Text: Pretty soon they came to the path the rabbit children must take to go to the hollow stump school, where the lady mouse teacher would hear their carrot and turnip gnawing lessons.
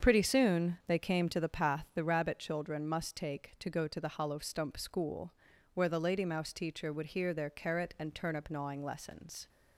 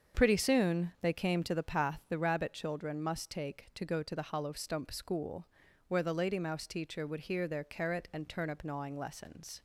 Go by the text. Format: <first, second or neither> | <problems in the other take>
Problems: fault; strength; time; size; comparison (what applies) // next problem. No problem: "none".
neither | starts louder than the rest; the same in both